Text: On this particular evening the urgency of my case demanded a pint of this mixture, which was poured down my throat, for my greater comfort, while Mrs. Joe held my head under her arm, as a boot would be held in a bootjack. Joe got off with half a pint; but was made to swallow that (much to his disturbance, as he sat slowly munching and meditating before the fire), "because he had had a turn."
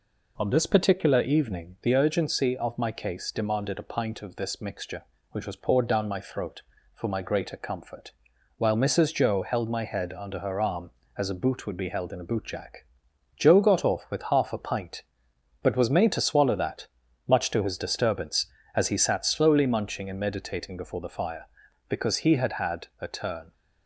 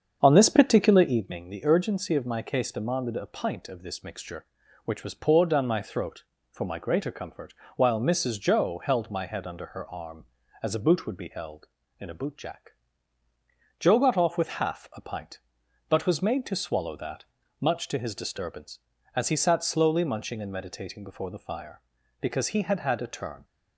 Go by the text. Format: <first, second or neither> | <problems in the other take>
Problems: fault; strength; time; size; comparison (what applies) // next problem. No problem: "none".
first | starts louder than the rest; strong; until 1.2 s; 7.5 dB